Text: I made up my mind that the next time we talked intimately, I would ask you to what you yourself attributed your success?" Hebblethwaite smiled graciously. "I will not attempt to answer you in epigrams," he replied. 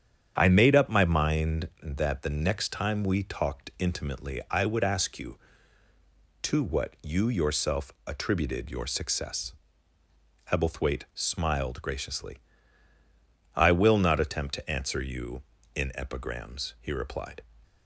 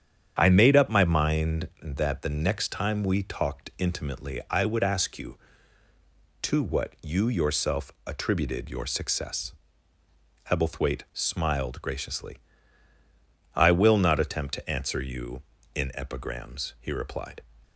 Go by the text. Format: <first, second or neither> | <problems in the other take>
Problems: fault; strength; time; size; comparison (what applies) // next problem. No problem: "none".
neither | starts louder than the rest; strong; the same in both // pauses between "yourself" and "attributed"; slight; the same in both